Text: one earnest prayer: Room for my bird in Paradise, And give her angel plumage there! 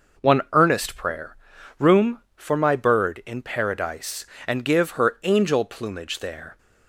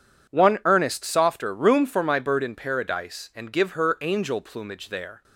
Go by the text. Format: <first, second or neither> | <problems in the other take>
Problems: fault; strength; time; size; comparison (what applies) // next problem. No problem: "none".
first | says "softer" for "prayer"; at 1.0 s